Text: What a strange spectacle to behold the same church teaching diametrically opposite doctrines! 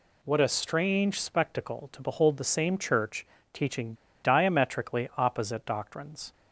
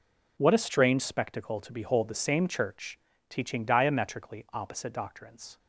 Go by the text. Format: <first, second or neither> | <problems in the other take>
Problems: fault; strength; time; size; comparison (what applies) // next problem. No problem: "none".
second | pauses between "church" and "teaching"; slight; at 3.2 s; 0.26 s long; slight in the second // pauses between "teaching" and "diametrically"; slight; at 3.9 s; 0.28 s long